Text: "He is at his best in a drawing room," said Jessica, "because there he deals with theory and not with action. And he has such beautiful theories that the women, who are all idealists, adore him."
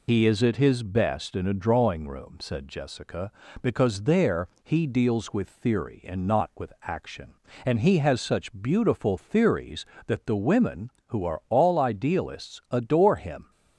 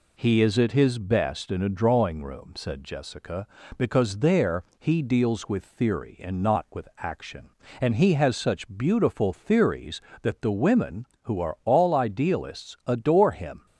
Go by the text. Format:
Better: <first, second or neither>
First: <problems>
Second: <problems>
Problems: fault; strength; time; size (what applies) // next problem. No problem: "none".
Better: second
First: loses the start of "He"; at 0.0 s; 60 ms // pauses between "there" and "he"; slight; at 4.4 s; 0.16 s long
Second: pauses between "there" and "he"; slight; at 4.6 s; 0.16 s long